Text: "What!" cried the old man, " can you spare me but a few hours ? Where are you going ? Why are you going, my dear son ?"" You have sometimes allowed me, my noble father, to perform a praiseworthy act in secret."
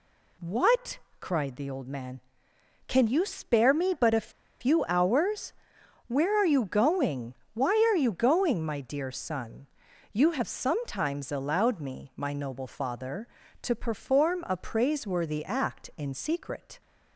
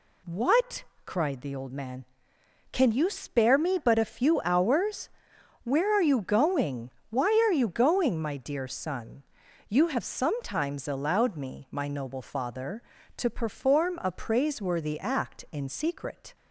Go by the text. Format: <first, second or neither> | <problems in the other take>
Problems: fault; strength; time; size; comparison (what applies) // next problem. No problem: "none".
second | pauses between "a" and "few"; slight; at 4.3 s; 0.30 s long